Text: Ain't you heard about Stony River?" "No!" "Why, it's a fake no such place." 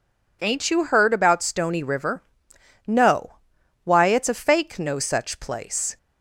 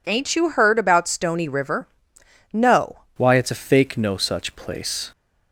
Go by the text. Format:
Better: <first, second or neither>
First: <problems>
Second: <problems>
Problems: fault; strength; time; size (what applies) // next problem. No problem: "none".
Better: first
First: none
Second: changes voice at "Why"; from 3.1 s on; 2.0 s long